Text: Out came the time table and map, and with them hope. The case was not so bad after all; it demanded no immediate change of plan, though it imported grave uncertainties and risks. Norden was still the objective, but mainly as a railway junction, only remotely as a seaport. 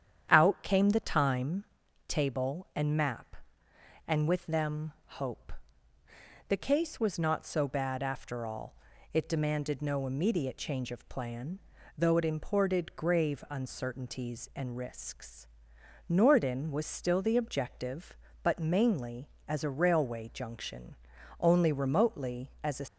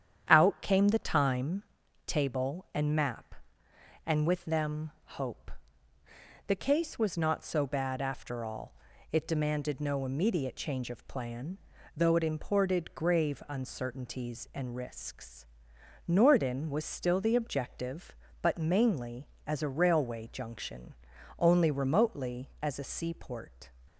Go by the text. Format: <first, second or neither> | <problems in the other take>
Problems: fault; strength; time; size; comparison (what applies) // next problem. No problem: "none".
second | starts louder than the rest; strong; until 1.3 s; 9 dB; strong in the second // pauses between "time" and "table"; at 1.6 s; 0.44 s long; also in the second // stops before "seaport"; at 22.8 s